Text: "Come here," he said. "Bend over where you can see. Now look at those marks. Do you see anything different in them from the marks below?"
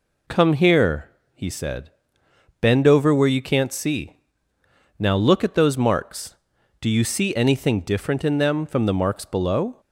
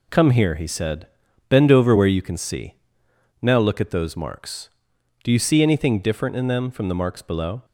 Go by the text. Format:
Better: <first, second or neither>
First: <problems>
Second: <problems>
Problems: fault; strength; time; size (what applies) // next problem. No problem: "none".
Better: second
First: says "can't" for "can"; at 3.4 s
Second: none